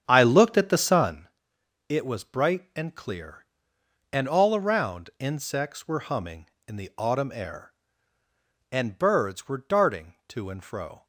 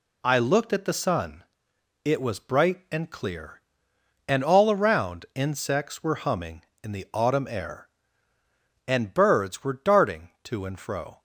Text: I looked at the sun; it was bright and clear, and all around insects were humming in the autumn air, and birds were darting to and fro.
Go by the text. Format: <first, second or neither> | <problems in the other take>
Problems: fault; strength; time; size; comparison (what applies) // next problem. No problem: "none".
second | starts louder than the rest; strong; until 1.3 s; 8 dB